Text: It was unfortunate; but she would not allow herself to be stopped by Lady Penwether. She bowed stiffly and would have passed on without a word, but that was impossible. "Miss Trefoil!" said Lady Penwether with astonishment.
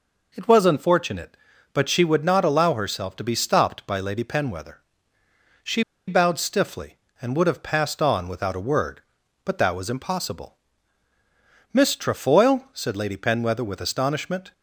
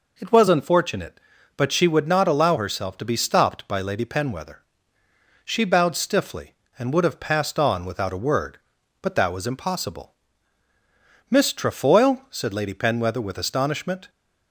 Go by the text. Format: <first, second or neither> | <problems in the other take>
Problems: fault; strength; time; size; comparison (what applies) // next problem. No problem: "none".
second | pauses between "She" and "bowed"; slight; at 5.8 s; 0.25 s long